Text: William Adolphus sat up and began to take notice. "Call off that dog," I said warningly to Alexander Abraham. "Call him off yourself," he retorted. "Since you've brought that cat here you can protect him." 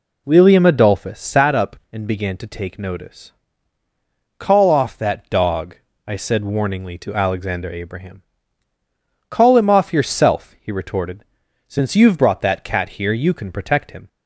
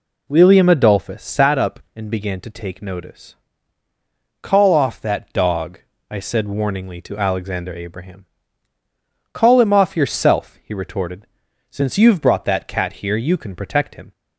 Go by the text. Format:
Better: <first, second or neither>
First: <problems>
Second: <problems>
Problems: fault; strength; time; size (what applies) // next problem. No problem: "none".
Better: neither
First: none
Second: none